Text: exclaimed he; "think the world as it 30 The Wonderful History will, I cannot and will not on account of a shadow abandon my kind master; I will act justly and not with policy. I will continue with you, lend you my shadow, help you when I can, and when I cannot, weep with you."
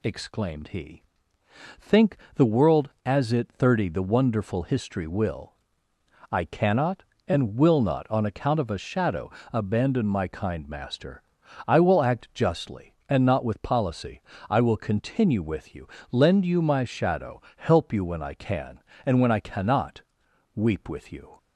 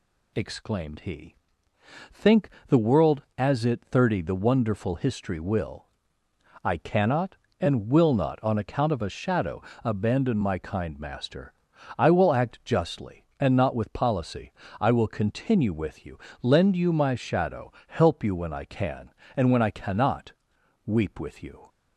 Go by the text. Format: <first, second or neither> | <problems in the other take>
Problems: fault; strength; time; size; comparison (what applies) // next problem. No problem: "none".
neither | pauses between "think" and "the"; slight; the same in both // pauses between "shadow" and "abandon"; slight; the same in both